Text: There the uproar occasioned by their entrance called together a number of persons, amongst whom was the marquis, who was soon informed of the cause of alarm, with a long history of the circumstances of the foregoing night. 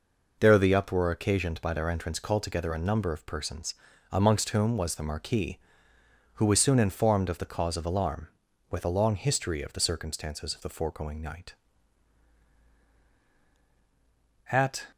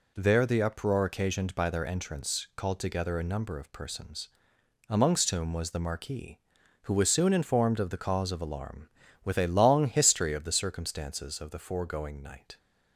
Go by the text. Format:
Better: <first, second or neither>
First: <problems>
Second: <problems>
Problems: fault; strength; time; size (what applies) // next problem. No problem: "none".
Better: second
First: goes on to say "At"; slight; from 14.5 s on; 0.34 s long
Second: none